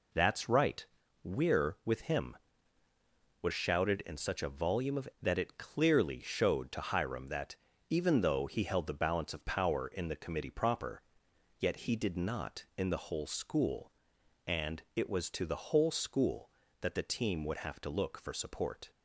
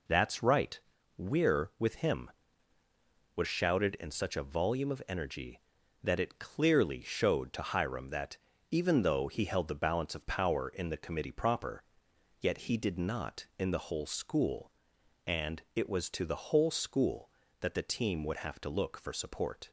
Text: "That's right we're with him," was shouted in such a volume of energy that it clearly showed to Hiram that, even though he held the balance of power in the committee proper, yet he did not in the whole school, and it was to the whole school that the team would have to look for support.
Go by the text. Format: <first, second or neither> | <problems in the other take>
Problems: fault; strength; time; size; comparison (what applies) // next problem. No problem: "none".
second | pauses between "right" and "we're"; at 0.8 s; 0.40 s long; also in the second // skips "energy"; at 5.1 s